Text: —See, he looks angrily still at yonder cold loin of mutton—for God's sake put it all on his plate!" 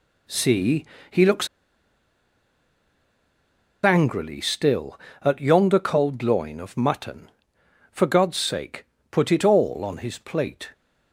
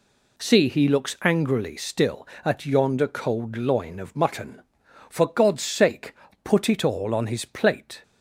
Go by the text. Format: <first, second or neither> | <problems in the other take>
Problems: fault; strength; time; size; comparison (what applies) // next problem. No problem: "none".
second | pauses between "looks" and "angrily"; strong; at 1.4 s; 2.3 s long // pauses between "sake" and "put"; slight; at 8.8 s; 0.26 s long; slight in the second